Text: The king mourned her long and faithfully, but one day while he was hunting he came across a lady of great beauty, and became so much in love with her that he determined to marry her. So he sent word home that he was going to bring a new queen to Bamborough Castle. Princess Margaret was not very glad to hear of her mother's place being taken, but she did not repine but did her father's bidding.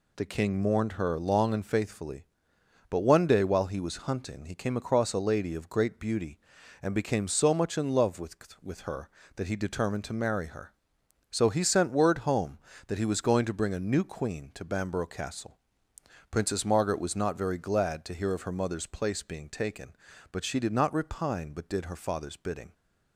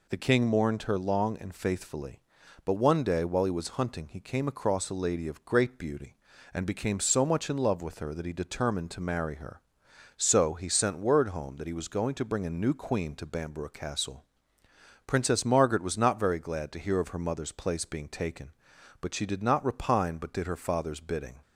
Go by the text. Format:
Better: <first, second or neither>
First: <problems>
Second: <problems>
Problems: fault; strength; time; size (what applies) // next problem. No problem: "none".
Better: second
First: says "with" twice; at 8.6 s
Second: none